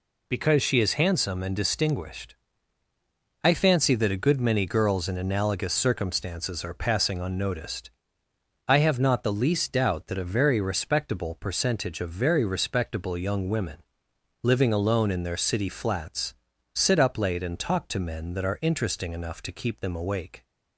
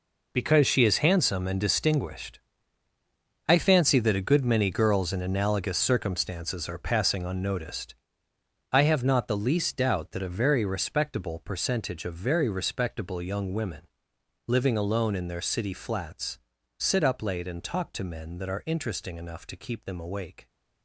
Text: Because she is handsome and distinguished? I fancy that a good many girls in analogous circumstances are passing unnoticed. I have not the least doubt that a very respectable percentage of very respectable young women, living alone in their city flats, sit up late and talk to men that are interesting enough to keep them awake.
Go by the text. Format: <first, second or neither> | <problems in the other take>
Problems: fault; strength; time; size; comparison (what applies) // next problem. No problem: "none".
first | gets quieter; strong; throughout; 12 dB